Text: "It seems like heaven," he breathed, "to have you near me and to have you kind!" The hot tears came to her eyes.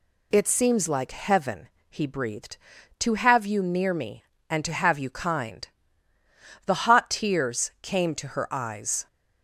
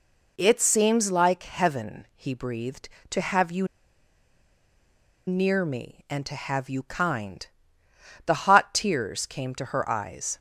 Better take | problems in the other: first | pauses between "you" and "near"; strong; at 3.6 s; 1.6 s long

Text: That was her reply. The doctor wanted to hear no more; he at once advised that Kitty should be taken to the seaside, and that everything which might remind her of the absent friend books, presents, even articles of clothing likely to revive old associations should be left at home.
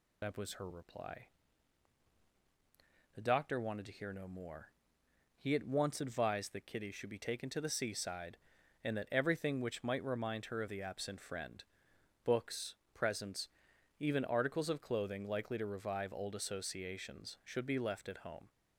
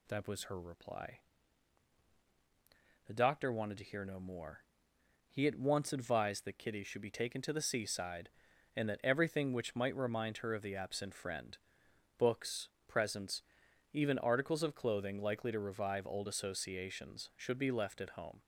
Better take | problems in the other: second | loses the start of "That"; at 0.2 s; 50 ms // pauses between "friend" and "books"; noticeable; at 11.6 s; 0.62 s long; noticeable in the second

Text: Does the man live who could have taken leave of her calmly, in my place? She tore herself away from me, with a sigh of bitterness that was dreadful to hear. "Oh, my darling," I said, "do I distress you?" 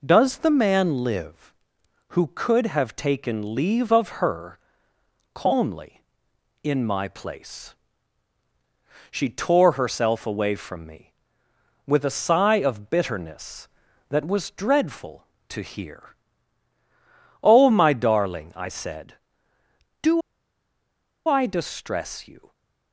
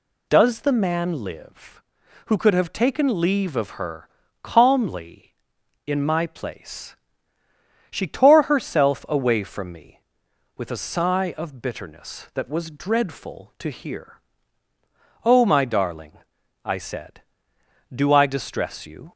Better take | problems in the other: second | pauses between "her" and "calmly"; noticeable; at 4.5 s; 0.74 s long; slight in the second // pauses between "do" and "I"; at 20.2 s; 1.0 s long

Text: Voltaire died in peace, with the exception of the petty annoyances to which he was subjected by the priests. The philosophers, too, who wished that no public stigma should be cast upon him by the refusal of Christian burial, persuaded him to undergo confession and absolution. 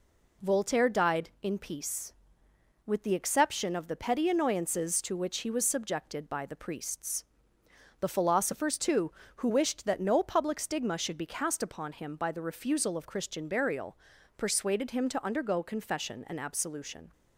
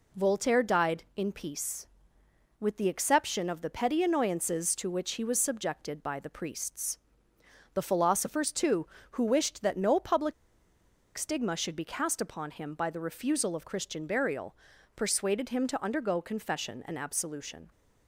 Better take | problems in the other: first | pauses between "public" and "stigma"; noticeable; at 10.3 s; 0.82 s long

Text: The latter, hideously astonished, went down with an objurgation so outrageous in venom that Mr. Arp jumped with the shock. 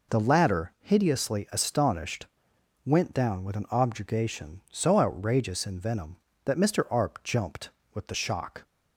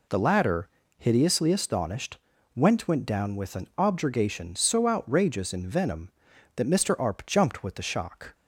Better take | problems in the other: first | says "went" twice; at 2.8 s

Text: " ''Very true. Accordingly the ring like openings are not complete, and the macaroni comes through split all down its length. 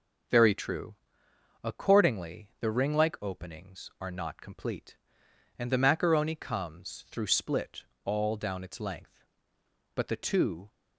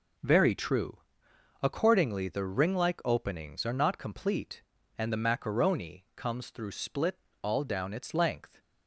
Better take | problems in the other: second | pauses between "split" and "all"; slight; at 7.8 s; 0.18 s long; slight in the second // goes on to say "But the two"; noticeable; from 9.9 s on; 0.74 s long

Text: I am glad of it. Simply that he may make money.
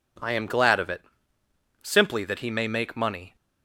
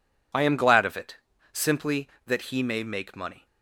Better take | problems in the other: neither | none

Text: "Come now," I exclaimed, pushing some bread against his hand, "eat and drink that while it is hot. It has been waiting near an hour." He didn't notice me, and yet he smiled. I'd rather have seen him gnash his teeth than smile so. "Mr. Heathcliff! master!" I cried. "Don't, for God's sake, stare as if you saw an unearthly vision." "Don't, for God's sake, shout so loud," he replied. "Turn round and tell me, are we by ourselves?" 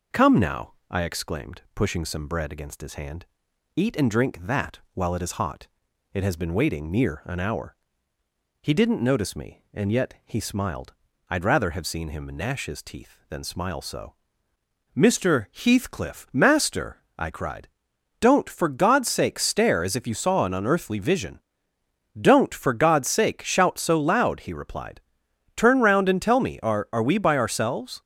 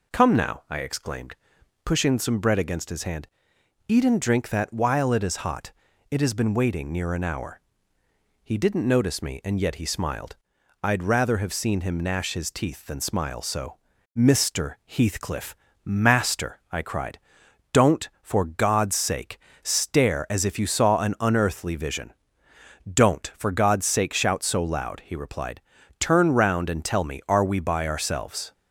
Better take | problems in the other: second | says "are" twice; at 26.9 s

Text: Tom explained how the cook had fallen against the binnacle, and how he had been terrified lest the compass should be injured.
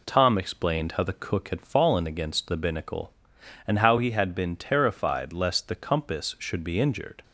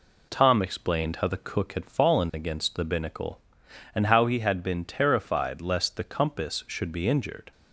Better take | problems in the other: neither | none

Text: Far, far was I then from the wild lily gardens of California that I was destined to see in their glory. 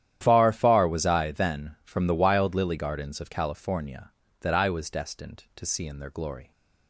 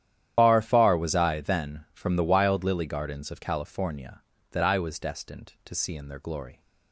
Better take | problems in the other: first | loses the start of "Far"; at 0.3 s; 80 ms // starts louder than the rest; strong; until 1.3 s; 10.5 dB; strong in the first

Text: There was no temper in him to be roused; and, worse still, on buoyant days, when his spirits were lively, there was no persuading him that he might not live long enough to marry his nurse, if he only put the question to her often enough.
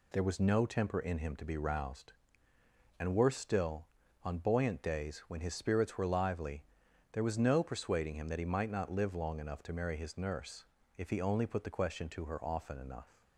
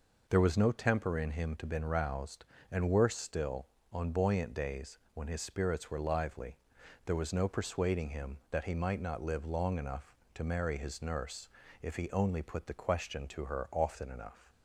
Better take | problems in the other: first | says "been" for "be"; at 1.6 s

